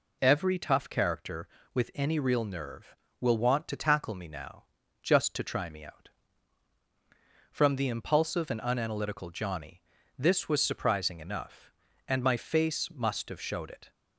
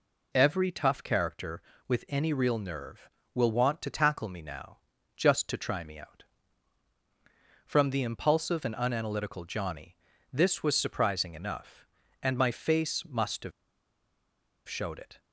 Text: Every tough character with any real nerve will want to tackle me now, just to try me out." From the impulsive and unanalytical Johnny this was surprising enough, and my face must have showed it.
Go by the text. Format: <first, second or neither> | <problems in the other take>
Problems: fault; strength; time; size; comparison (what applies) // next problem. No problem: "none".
first | pauses between "Johnny" and "this"; slight; at 9.9 s; 0.34 s long; slight in the first // pauses between "have" and "showed"; at 13.5 s; 1.1 s long